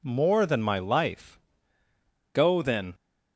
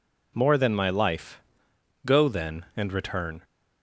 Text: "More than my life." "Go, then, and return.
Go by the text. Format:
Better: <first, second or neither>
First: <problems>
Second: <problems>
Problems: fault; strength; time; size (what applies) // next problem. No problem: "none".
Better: second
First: stops before "and return"; at 2.9 s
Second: none